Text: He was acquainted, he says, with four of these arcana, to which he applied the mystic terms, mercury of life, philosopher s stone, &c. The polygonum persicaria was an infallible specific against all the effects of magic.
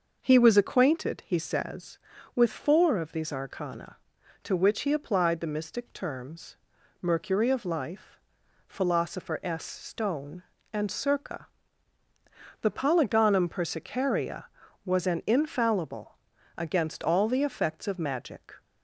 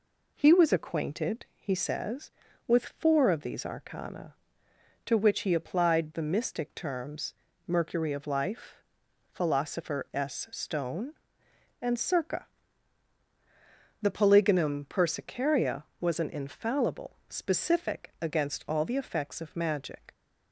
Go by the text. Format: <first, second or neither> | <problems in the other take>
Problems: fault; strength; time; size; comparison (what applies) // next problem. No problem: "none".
second | skips "specific"; at 16.3 s